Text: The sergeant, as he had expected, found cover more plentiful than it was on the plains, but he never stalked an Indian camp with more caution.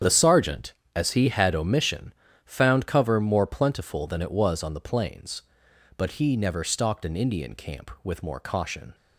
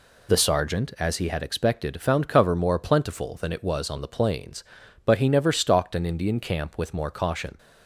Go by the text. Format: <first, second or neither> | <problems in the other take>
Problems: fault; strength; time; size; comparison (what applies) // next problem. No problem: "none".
second | starts louder than the rest; strong; until 1.2 s; 8.5 dB // says "omission" for "expected"; at 1.5 s